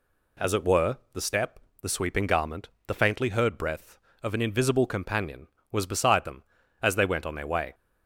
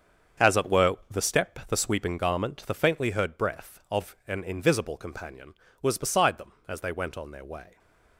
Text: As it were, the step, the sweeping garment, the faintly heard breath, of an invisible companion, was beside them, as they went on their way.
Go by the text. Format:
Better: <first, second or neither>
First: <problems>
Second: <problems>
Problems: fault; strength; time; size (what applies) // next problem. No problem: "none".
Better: first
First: none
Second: gets quieter; strong; throughout; 10.5 dB // stays silent after the last word; slight; from 7.6 s on; 0.5 s long